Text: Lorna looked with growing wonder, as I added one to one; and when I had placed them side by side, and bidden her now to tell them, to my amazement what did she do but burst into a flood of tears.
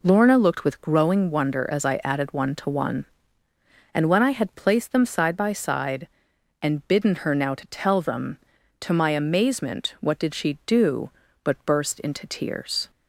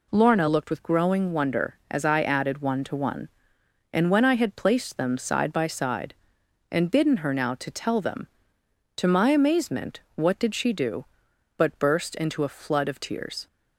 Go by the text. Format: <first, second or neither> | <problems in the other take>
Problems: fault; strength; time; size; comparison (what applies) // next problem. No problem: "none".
second | skips "a flood of"; at 12.2 s